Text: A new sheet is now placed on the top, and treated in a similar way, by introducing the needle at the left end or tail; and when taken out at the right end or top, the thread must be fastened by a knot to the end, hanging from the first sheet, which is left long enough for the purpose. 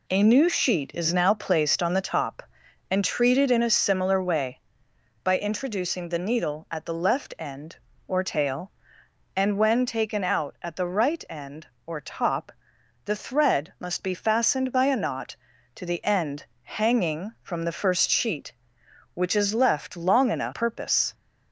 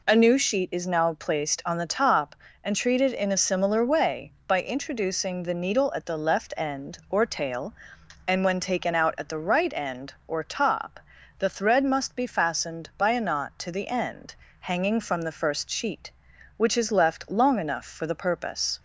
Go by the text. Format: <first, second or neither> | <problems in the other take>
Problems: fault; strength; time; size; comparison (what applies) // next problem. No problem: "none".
second | skips "for the"; at 20.5 s